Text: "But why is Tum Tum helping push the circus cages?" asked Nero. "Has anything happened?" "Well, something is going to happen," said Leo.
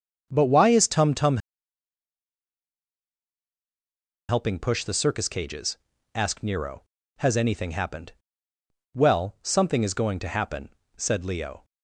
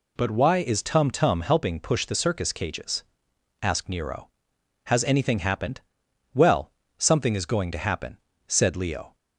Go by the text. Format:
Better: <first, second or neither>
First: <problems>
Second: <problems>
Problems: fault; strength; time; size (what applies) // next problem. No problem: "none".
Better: second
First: starts louder than the rest; until 1.3 s; 6.5 dB // pauses between "Tum" and "helping"; strong; at 1.3 s; 2.9 s long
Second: none